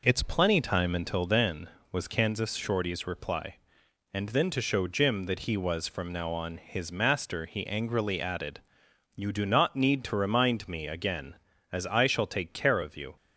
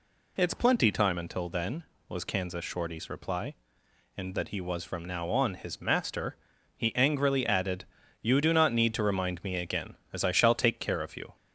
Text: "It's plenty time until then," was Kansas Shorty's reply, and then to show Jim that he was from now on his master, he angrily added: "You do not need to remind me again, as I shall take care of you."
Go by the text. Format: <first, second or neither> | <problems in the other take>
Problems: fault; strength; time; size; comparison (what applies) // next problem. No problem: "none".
first | skips "then to show Jim"; at 4.3 s